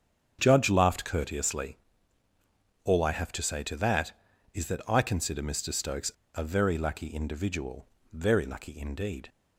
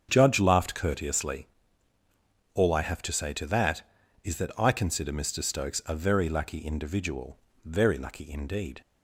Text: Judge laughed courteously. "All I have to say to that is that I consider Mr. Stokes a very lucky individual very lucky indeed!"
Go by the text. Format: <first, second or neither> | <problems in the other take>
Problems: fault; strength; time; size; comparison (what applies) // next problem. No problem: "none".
second | starts louder than the rest; strong; until 1.4 s; 8.5 dB; strong in the second // pauses between "Stokes" and "a"; slight; at 6.1 s; 0.22 s long // pauses between "individual" and "very"; slight; at 7.8 s; 0.24 s long; slight in the second